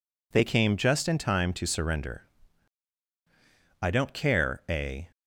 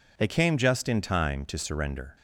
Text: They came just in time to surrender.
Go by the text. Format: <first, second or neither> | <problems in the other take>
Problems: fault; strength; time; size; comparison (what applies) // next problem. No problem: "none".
second | goes on to say "I don't care a"; from 3.7 s on; 1.3 s long